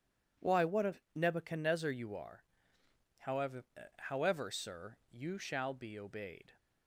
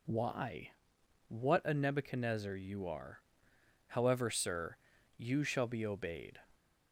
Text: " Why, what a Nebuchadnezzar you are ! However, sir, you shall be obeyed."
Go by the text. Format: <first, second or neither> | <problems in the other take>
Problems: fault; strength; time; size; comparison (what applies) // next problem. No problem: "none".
second | pauses between "a" and "Nebuchadnezzar"; slight; at 0.9 s; 0.22 s long // says "However" twice; at 3.9 s